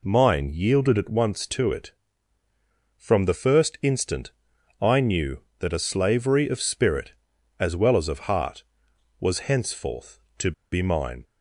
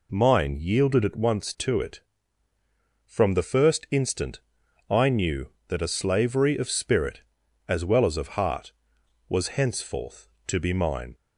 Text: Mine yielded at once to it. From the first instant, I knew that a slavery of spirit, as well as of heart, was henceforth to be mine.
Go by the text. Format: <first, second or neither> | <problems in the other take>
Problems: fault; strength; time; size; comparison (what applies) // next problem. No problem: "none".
second | pauses between "to" and "be"; slight; at 10.5 s; 0.20 s long